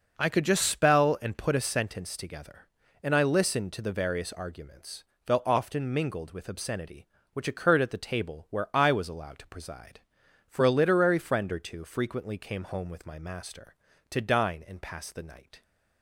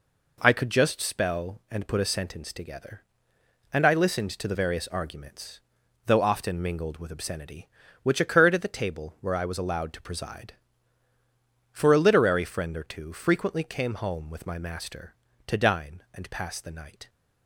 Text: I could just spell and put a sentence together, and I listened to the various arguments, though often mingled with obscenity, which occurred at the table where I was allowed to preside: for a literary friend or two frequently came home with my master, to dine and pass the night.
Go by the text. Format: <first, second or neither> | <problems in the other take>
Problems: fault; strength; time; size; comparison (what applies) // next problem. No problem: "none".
neither | none